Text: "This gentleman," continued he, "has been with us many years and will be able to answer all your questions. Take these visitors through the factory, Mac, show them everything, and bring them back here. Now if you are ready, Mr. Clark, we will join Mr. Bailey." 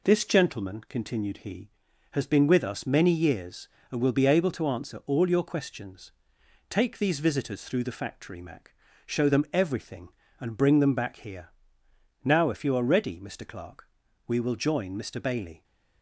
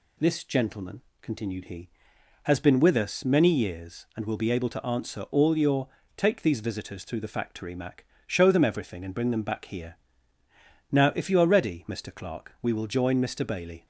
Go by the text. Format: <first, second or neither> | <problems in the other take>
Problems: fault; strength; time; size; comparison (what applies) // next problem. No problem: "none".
first | skips "questions"; at 6.0 s